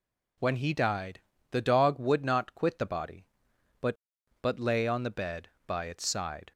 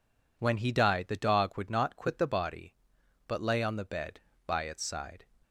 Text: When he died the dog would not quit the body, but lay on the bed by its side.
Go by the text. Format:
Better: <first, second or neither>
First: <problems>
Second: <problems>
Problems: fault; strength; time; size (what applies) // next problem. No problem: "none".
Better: second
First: pauses between "died" and "the"; slight; at 1.1 s; 0.30 s long // says "but" twice; at 4.3 s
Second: none